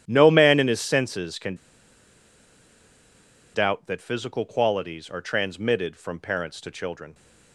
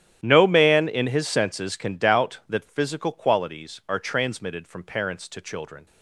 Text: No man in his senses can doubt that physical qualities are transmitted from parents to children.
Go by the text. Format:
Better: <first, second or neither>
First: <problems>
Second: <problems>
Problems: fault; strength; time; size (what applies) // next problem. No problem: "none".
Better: second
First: starts louder than the rest; strong; until 1.0 s; 10.5 dB // pauses between "can" and "doubt"; strong; at 1.5 s; 1.9 s long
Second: starts louder than the rest; strong; until 1.2 s; 11 dB